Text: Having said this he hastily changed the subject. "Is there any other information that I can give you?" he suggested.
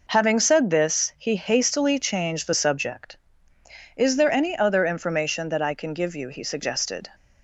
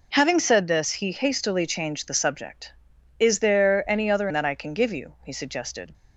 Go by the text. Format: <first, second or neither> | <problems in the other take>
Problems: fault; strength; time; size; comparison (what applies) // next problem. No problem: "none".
first | skips "information"; at 4.2 s